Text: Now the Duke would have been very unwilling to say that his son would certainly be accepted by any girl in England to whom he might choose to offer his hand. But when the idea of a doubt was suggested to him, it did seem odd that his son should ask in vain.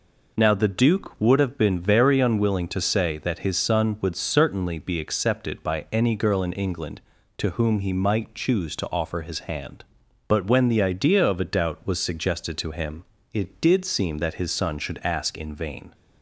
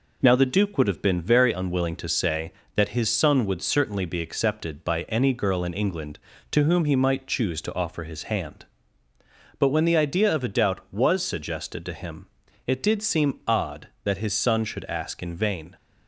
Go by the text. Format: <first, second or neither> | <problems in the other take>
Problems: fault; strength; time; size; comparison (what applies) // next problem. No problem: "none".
second | skips "odd"; at 14.1 s